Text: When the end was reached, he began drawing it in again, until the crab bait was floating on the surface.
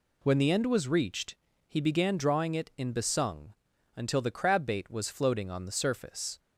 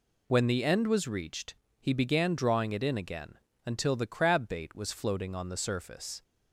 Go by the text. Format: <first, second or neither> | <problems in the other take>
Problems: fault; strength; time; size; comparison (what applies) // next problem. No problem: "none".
second | says "besung" for "again"; at 2.9 s